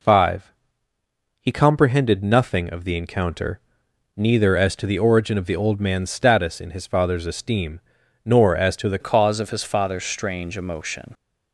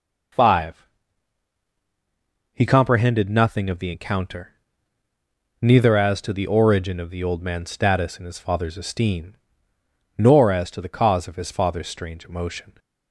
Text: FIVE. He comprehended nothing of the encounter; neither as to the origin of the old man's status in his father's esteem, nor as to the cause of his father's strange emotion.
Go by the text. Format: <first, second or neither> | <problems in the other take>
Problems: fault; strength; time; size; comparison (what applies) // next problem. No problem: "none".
second | changes voice at "cause"; from 9.0 s on; 2.1 s long